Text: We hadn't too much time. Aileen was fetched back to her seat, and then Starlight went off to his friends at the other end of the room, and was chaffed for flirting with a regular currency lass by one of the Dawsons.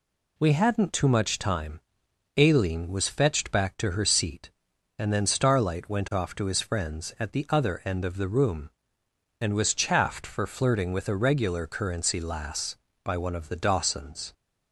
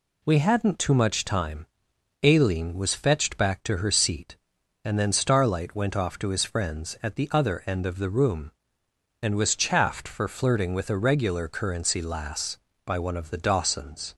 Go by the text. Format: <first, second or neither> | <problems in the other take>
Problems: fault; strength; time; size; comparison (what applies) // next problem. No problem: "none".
neither | none